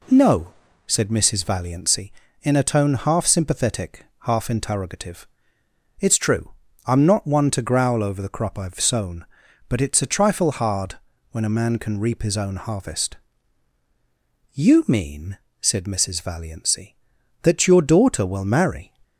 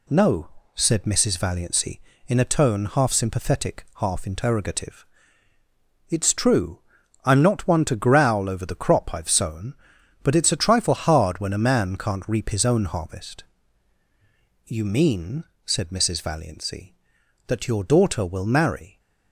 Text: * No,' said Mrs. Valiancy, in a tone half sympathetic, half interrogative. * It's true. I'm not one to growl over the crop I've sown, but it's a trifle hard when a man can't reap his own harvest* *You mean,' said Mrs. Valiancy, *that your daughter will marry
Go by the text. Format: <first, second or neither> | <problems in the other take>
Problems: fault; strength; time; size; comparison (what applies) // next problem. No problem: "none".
second | pauses between "hard" and "when"; slight; at 10.9 s; 0.36 s long // says "can" for "can't"; at 11.7 s // pauses between "harvest" and "You"; strong; at 13.1 s; 1.3 s long; also in the second